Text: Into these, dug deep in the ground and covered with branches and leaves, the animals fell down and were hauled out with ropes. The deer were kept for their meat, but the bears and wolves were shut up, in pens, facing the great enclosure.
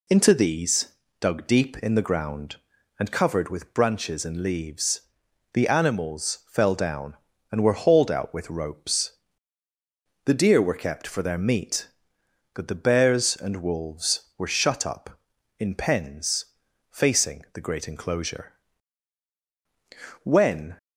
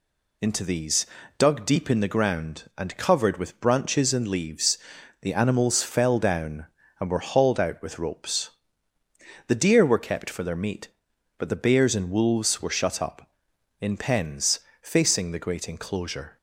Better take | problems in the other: second | goes on to say "When"; from 20.2 s on; 0.54 s long

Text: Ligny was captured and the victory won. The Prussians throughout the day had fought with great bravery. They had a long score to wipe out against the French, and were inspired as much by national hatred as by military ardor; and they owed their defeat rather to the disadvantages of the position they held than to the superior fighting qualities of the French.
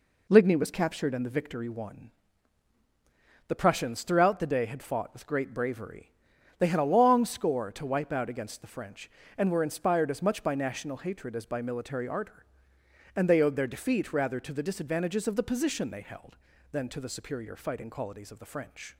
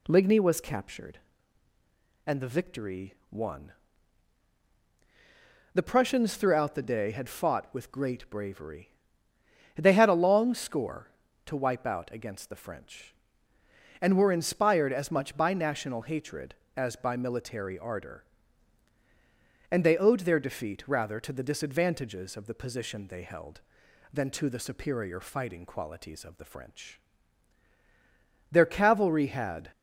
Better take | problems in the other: first | pauses between "victory" and "won"; slight; at 3.1 s; 0.18 s long // goes on to say "Their cavalry had"; noticeable; from 28.4 s on; 1.2 s long

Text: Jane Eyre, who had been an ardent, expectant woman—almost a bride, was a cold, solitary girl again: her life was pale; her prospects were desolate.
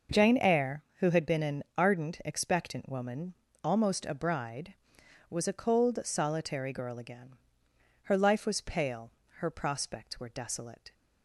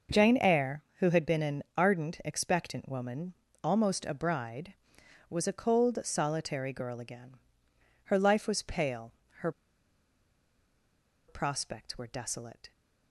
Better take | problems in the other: first | pauses between "an" and "ardent"; slight; at 1.6 s; 0.16 s long; slight in the first // pauses between "her" and "prospects"; strong; at 9.5 s; 1.7 s long

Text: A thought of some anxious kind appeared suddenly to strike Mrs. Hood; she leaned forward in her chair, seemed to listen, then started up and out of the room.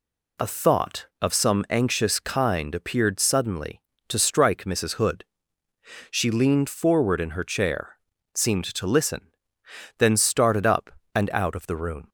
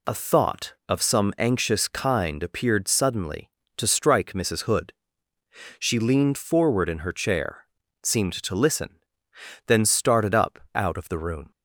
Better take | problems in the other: first | skips "and"; at 10.6 s

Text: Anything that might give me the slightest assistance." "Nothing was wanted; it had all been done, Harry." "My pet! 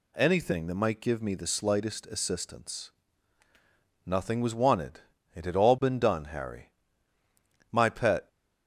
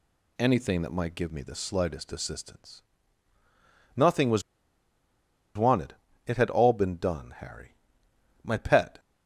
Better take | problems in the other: first | pauses between "was" and "wanted"; at 4.4 s; 1.1 s long

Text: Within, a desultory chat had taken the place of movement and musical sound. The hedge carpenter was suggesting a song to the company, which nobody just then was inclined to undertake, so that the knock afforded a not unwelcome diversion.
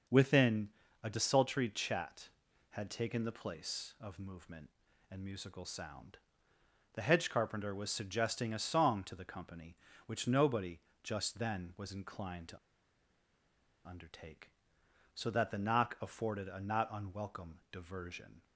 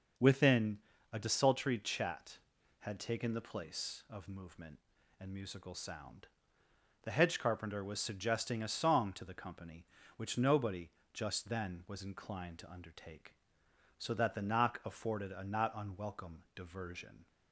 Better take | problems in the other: second | starts louder than the rest; until 1.4 s; 6 dB; also in the second // pauses between "nobody" and "just"; slight; at 10.7 s; 0.24 s long; slight in the second // pauses between "to" and "undertake"; strong; at 12.5 s; 1.2 s long // pauses between "unwelcome" and "diversion"; slight; at 17.5 s; 0.16 s long; slight in the second

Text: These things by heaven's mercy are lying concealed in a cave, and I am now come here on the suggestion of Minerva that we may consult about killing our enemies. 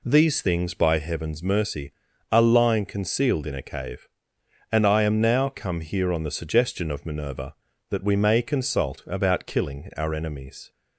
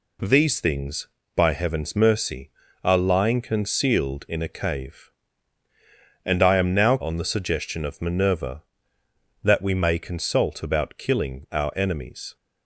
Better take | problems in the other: first | skips "come here"; at 7.0 s

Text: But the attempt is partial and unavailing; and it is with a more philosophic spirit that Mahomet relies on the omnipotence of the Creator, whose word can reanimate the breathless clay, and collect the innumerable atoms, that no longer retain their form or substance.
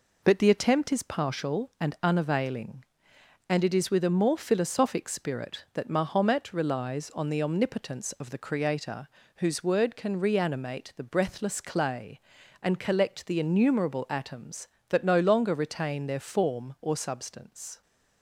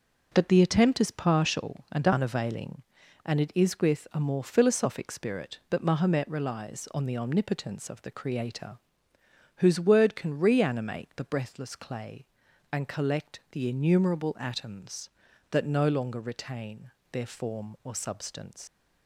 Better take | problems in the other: first | pauses between "retain" and "their"; slight; at 16.9 s; 0.20 s long // leaves "substance" unfinished; at 18.6 s; 110 ms

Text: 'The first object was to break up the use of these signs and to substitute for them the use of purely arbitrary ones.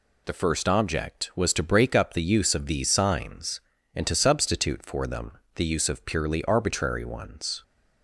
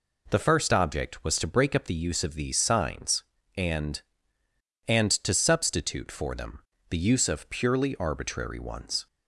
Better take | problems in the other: first | says "and" twice; at 4.8 s // pauses between "them" and "the"; slight; at 6.6 s; 0.28 s long; slight in the first

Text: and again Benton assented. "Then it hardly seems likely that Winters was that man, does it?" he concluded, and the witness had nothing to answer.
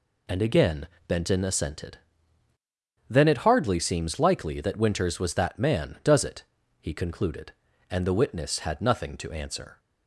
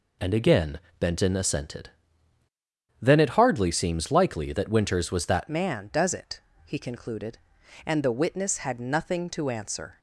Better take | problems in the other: first | pauses between "again" and "Benton"; slight; at 0.7 s; 0.22 s long; slight in the first // changes voice at "man"; from 5.4 s on; 4.5 s long

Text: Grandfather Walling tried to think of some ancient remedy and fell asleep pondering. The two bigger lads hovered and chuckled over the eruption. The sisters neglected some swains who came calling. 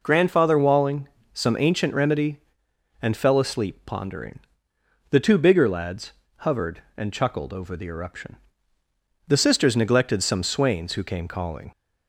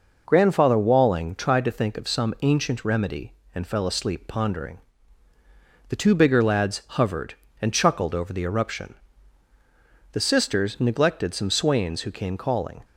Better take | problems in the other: second | skips "tried to think of"; at 1.2 s // pauses between "lads" and "hovered"; slight; at 6.1 s; 0.26 s long

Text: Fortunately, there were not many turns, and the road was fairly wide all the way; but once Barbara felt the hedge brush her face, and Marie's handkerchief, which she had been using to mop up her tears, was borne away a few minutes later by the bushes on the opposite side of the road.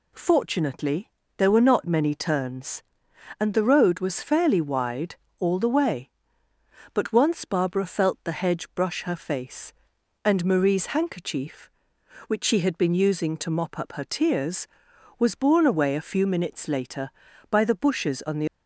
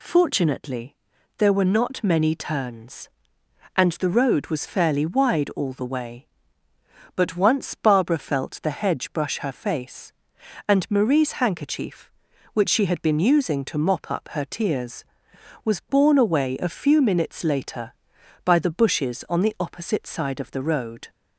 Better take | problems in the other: second | pauses between "wide" and "all"; slight; at 5.1 s; 0.24 s long // stops before "opposite side of the road"; at 18.4 s

